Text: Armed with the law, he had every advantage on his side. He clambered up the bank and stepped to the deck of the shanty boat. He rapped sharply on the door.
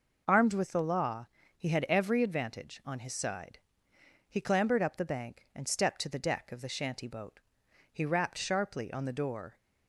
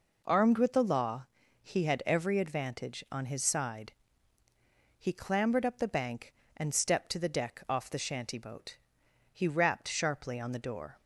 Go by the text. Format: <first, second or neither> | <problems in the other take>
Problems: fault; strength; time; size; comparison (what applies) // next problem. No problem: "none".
first | says "off" for "of"; at 7.6 s